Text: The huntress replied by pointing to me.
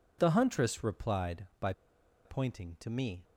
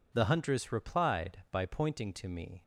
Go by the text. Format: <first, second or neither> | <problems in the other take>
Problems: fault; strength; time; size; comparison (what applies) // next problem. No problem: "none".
second | pauses between "by" and "pointing"; noticeable; at 1.7 s; 0.53 s long